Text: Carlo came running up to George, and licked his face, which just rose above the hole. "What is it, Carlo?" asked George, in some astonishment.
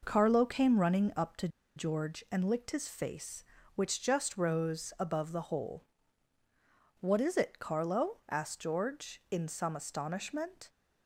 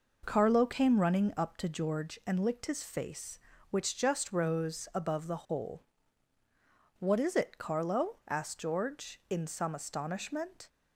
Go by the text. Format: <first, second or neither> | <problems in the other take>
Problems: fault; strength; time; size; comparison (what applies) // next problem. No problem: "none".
second | pauses between "to" and "George"; slight; at 1.4 s; 0.28 s long